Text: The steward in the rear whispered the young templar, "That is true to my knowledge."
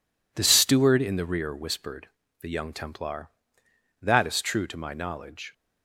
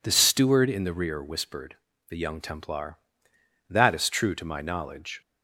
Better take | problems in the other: second | gets quieter; strong; throughout; 8.5 dB // pauses between "whispered" and "the"; slight; at 2.0 s; 0.32 s long; slight in the second

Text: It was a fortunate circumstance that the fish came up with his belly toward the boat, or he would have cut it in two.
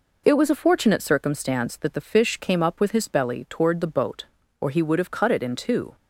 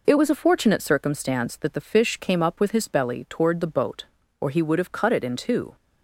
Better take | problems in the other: neither | none

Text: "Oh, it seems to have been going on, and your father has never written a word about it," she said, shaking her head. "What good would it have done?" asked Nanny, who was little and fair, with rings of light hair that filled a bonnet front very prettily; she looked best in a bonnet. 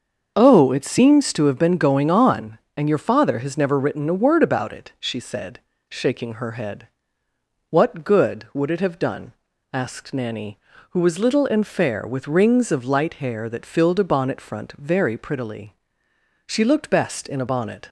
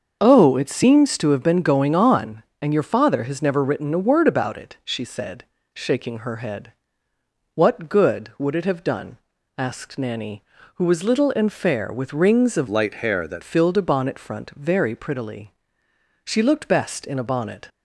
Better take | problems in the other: first | starts louder than the rest; until 1.2 s; 6.5 dB; also in the first // changes voice from "light" to "that"; from 12.6 to 13.4 s; 0.8 s long

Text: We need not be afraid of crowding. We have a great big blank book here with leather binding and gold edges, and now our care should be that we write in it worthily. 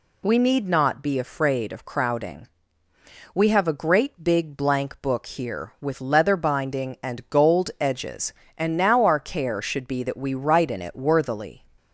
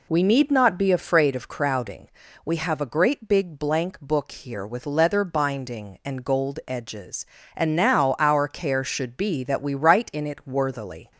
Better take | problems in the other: first | starts louder than the rest; slight; until 1.3 s; 3 dB

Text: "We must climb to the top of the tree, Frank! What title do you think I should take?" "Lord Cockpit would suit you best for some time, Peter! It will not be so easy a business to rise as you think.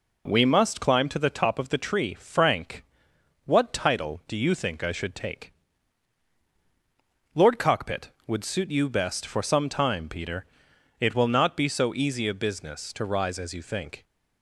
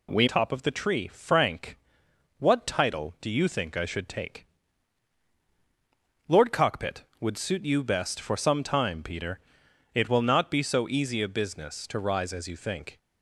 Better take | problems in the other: first | skips "must climb to the"; at 0.2 s

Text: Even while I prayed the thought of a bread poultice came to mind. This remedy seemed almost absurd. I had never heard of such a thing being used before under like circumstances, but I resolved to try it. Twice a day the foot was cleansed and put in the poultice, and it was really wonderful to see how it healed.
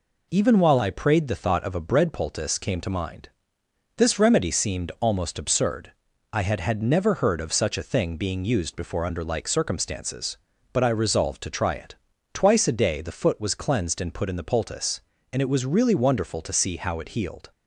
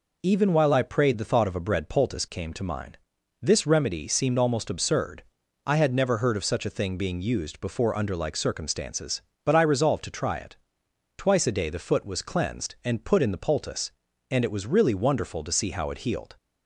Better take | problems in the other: second | says "had" twice; at 6.5 s

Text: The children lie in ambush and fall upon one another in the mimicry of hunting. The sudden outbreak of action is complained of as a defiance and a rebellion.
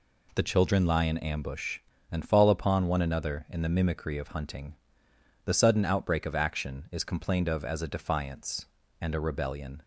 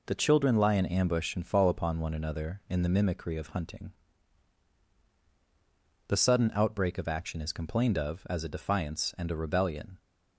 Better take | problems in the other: neither | none

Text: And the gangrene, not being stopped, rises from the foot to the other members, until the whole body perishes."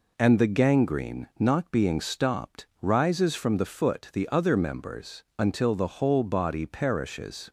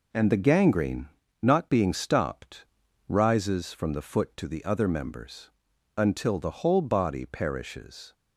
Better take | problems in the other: second | skips "to"; at 4.1 s

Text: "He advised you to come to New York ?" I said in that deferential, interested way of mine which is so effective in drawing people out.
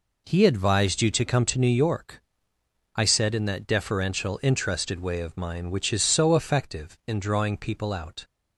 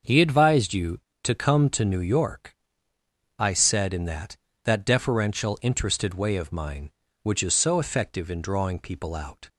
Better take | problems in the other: first | starts louder than the rest; until 1.2 s; 6.5 dB // says "that" twice; at 4.6 s

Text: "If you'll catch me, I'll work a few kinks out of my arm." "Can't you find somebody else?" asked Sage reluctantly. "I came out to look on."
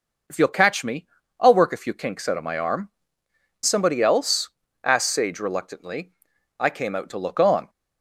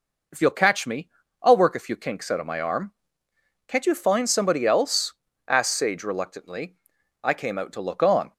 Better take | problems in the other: second | skips "Can't you find"; at 3.2 s

